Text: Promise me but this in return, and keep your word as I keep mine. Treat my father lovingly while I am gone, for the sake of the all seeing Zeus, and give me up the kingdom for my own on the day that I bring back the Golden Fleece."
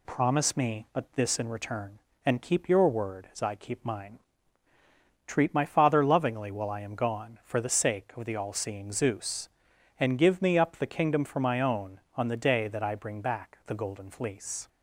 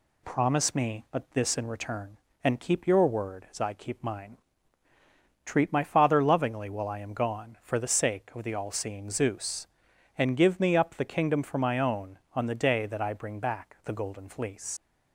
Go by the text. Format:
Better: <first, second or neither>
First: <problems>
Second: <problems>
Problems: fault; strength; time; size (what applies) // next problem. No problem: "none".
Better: first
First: none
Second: leaves "Fleece" unfinished; at 14.7 s; 95 ms